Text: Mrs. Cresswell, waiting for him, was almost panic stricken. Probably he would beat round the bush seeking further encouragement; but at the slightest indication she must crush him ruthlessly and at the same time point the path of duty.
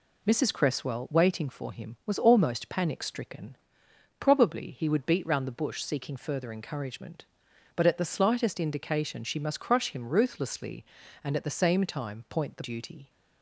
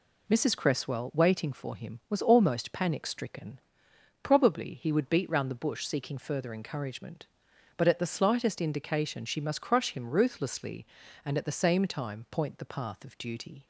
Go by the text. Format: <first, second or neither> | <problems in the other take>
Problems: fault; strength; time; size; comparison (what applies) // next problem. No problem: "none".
second | skips "path of"; at 12.6 s